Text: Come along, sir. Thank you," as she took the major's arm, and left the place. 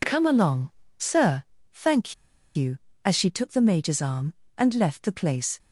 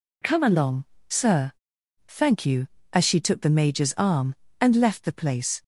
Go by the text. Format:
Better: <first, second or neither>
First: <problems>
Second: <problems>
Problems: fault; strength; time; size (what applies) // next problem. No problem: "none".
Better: second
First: pauses between "Thank" and "you"; at 2.1 s; 0.41 s long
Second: none